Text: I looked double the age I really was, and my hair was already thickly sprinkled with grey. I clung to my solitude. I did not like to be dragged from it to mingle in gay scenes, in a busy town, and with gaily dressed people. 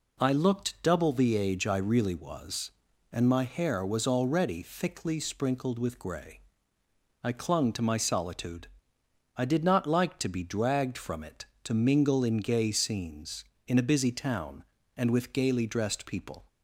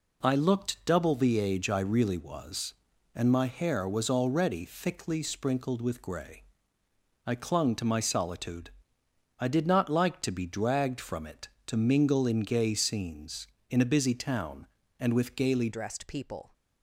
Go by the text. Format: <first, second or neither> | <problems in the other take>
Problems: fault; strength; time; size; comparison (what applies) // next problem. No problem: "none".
first | changes voice at "dressed"; from 15.7 s on; 0.8 s long